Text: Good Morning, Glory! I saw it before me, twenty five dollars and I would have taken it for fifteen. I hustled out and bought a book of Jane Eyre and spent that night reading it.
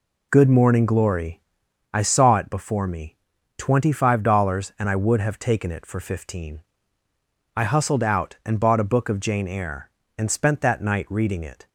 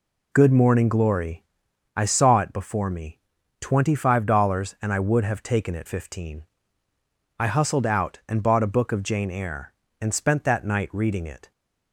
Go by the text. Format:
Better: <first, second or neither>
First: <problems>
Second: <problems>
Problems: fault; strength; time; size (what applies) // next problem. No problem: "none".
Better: first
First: none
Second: skips "for"; at 5.8 s